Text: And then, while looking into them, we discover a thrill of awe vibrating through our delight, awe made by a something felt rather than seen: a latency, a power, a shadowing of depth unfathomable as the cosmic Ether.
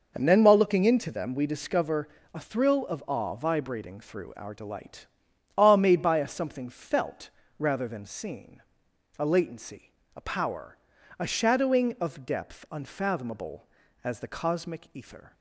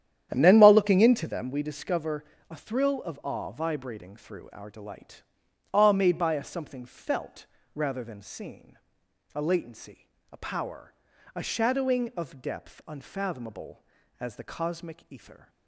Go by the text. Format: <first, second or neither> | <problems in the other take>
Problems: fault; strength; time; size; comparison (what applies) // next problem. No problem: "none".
first | starts louder than the rest; strong; until 1.6 s; 10 dB // pauses between "discover" and "a"; slight; at 2.2 s; 0.26 s long; slight in the first // pauses between "felt" and "rather"; slight; at 7.4 s; 0.28 s long; slight in the first